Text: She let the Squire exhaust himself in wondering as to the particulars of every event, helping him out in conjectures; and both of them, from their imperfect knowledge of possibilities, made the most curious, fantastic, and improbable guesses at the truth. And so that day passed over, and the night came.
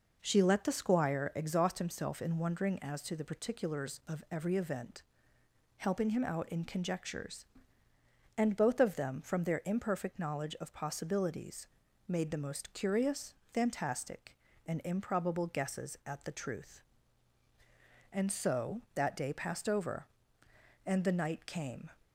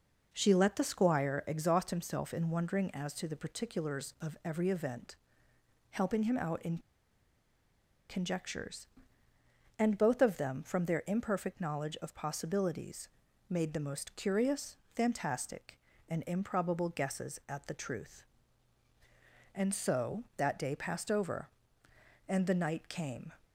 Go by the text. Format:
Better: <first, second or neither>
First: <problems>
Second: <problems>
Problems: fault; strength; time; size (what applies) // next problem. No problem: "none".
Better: first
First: none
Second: pauses between "in" and "conjectures"; strong; at 6.7 s; 1.3 s long